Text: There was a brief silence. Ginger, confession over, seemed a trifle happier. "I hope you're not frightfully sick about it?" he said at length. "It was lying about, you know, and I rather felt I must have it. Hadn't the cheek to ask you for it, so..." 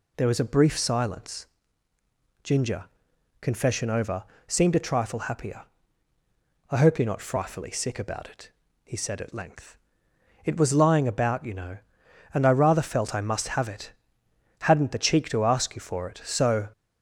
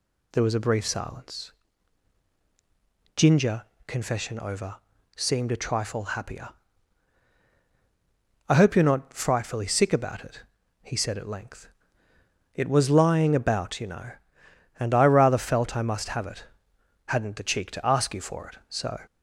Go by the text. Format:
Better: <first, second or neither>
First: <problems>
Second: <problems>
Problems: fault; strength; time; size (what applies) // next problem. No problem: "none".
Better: neither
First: none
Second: none